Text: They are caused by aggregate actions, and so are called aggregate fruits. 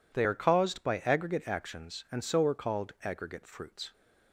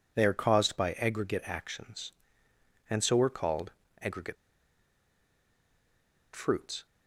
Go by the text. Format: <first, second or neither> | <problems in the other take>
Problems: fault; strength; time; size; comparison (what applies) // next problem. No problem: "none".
first | pauses between "called" and "aggregate"; slight; at 3.7 s; 0.30 s long // pauses between "aggregate" and "fruits"; strong; at 4.3 s; 1.9 s long